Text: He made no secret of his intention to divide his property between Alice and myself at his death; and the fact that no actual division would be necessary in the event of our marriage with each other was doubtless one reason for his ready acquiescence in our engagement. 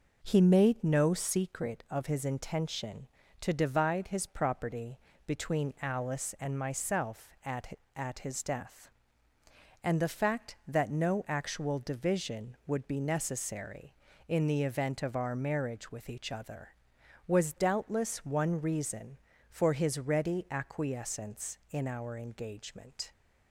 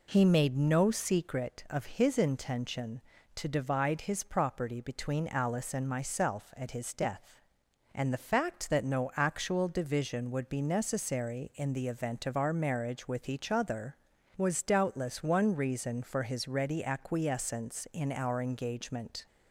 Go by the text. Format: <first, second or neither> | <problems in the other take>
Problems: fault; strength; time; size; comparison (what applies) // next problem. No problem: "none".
second | pauses between "property" and "between"; slight; at 4.9 s; 0.26 s long // says "at" twice; at 7.9 s